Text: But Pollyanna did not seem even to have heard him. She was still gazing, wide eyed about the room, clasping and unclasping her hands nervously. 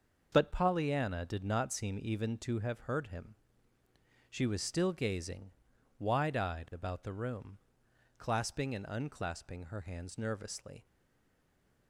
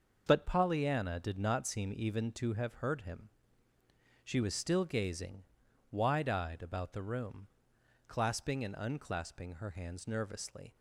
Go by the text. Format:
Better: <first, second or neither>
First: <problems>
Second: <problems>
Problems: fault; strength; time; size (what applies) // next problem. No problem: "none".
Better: second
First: starts louder than the rest; noticeable; until 1.3 s; 6 dB // stays silent after the last word; from 10.8 s on; 1.0 s long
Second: starts louder than the rest; noticeable; until 1.2 s; 6 dB